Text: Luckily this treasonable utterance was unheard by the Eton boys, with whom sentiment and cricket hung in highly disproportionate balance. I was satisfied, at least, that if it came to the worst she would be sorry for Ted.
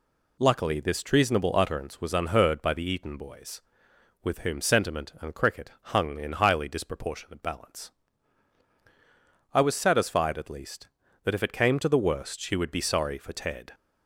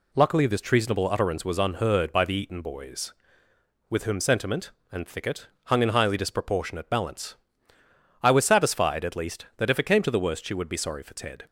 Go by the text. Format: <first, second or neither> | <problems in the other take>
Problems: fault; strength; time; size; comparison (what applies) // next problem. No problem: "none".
first | says "thicket" for "cricket"; at 5.0 s